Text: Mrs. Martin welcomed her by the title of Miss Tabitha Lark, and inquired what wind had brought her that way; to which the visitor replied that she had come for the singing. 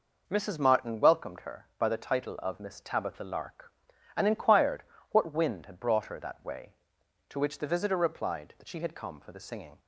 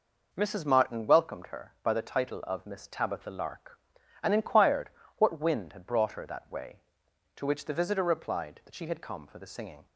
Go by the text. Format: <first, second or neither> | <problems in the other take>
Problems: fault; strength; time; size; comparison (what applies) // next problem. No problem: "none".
neither | pauses between "inquired" and "what"; slight; the same in both